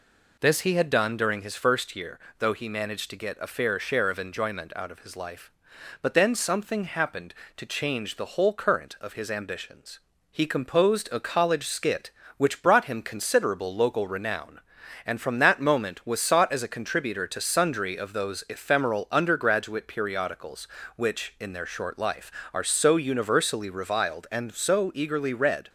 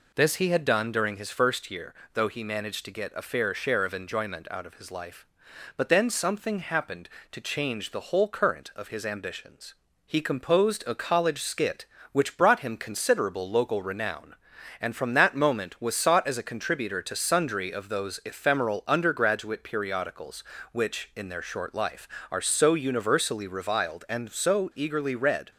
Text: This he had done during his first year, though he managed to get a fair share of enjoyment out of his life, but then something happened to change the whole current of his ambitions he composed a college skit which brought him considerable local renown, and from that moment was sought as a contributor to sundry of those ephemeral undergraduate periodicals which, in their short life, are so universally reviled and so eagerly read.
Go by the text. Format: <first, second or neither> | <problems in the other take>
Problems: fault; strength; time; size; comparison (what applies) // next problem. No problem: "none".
neither | pauses between "ambitions" and "he"; slight; the same in both